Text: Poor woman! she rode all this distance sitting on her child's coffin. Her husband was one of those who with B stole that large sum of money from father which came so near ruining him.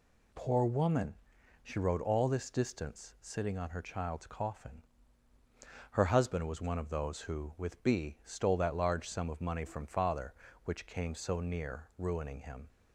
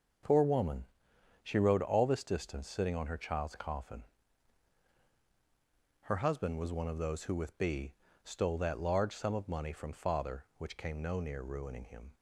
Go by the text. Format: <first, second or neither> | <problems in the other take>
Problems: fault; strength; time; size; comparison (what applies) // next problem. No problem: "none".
first | starts louder than the rest; until 1.7 s; 6.5 dB // pauses between "B" and "stole"; slight; at 7.9 s; 0.32 s long // says "no" for "so"; at 11.0 s